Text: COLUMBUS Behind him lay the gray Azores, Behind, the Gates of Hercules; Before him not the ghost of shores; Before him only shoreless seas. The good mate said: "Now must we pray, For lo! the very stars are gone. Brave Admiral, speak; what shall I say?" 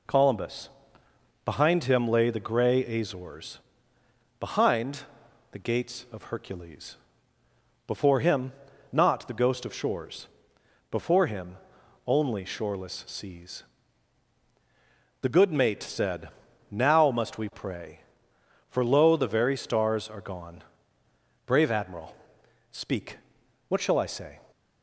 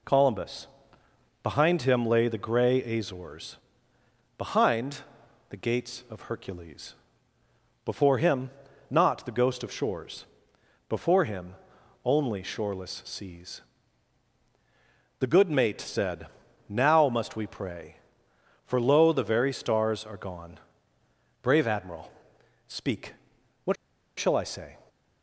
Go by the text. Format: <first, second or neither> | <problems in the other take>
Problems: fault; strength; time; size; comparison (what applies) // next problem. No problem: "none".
first | pauses between "COLUMBUS" and "Behind"; noticeable; at 0.6 s; 0.76 s long; noticeable in the first // pauses between "him" and "not"; at 8.4 s; 0.40 s long; also in the first // pauses between "him" and "only"; noticeable; at 11.5 s; 0.50 s long; noticeable in the first // pauses between "what" and "shall"; at 23.7 s; 0.43 s long